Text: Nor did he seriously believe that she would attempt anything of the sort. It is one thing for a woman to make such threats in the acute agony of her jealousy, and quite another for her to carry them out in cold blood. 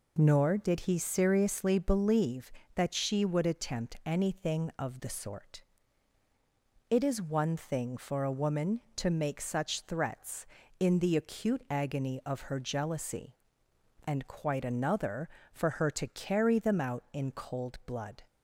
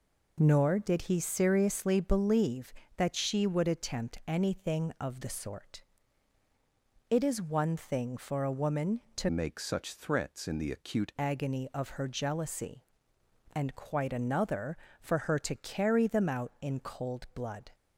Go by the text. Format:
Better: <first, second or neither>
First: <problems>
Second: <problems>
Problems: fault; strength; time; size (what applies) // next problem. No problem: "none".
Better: first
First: none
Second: changes voice from "make" to "acute"; from 9.2 to 11.1 s; 1.9 s long